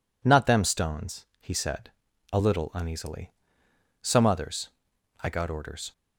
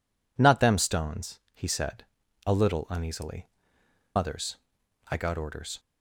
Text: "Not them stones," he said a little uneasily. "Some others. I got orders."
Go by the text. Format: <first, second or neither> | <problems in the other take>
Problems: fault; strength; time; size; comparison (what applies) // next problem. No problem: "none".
first | pauses between "said" and "a"; at 2.0 s; 0.38 s long; also in the first // skips "Some"; at 3.8 s